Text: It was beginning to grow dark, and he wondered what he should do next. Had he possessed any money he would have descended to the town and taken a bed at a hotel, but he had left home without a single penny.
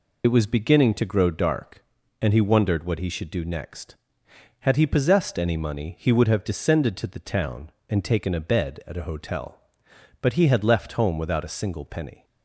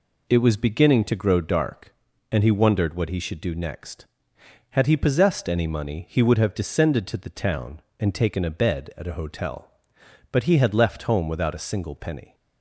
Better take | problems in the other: second | loses the start of "It"; at 0.2 s; 65 ms

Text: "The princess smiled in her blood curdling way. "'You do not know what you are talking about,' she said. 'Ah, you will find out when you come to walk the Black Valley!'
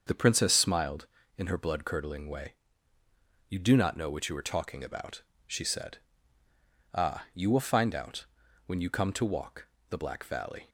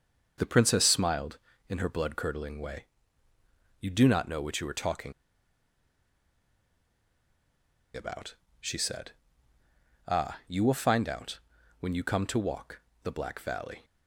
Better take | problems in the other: first | starts louder than the rest; until 1.6 s; 6.5 dB; also in the first // pauses between "talking" and "about"; strong; at 5.1 s; 2.8 s long // pauses between "out" and "when"; at 11.3 s; 0.42 s long; also in the first // pauses between "walk" and "the"; slight; at 12.8 s; 0.22 s long; slight in the first

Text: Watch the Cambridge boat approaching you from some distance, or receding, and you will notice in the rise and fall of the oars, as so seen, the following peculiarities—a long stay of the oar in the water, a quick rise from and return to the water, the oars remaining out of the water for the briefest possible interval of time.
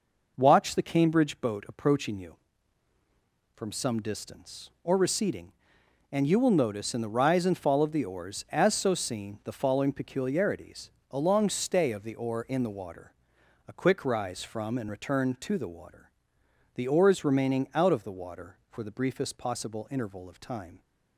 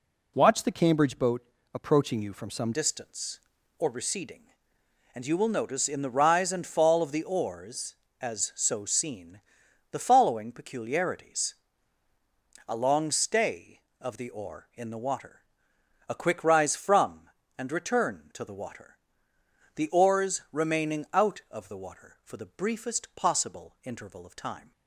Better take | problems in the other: first | pauses between "boat" and "approaching"; slight; at 1.4 s; 0.32 s long // changes voice at "distance"; from 2.7 s on; 22.0 s long

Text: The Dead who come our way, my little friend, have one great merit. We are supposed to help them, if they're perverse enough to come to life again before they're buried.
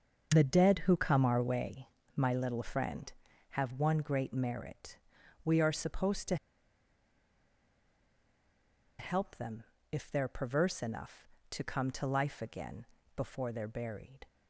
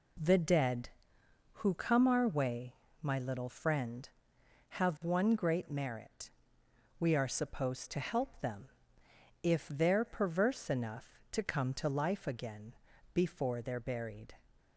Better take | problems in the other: second | starts louder than the rest; until 1.3 s; 6.5 dB // pauses between "to" and "help"; strong; at 6.3 s; 2.6 s long // pauses between "again" and "before"; slight; at 12.8 s; 0.32 s long; also in the second

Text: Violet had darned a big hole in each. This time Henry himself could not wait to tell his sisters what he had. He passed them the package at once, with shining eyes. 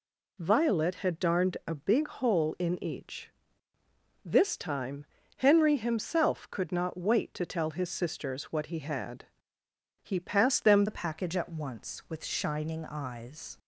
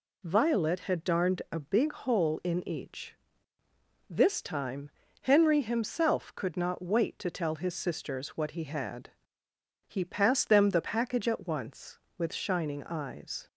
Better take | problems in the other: second | pauses between "time" and "Henry"; slight; at 5.0 s; 0.32 s long; slight in the second // changes voice at "the"; from 10.8 s on; 2.7 s long

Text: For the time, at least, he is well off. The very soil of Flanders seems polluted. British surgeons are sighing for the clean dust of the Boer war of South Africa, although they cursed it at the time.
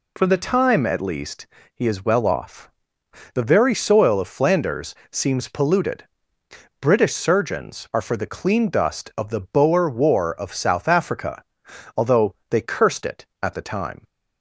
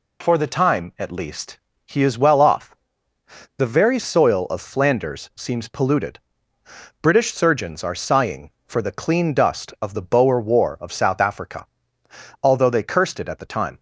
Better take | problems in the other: second | pauses between "Flanders" and "seems"; slight; at 4.9 s; 0.16 s long // skips "sighing"; at 8.0 s // pauses between "although" and "they"; slight; at 12.3 s; 0.16 s long

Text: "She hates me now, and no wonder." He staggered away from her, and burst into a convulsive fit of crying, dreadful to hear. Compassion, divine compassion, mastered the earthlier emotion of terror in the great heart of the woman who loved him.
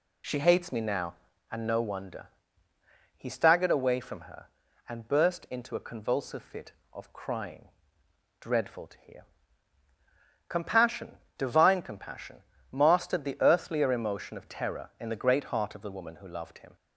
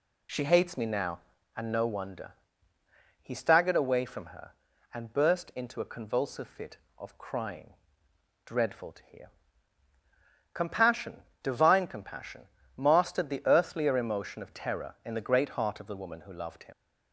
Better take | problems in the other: first | leaves "him" unfinished; at 16.7 s; 75 ms

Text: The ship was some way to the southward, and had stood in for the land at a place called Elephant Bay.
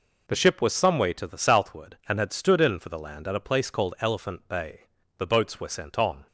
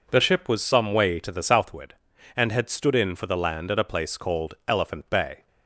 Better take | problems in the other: second | goes on to say "The boats were sent on"; noticeable; from 5.1 s on; 1.0 s long

